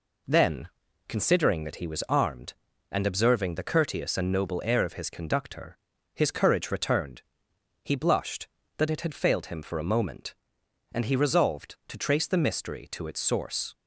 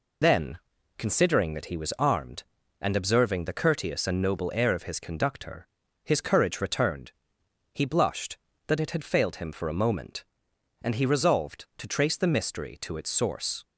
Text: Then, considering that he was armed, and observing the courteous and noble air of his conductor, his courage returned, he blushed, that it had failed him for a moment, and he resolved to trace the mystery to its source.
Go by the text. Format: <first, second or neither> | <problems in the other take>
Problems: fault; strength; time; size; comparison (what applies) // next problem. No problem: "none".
first | loses the start of "Then"; at 0.2 s; 55 ms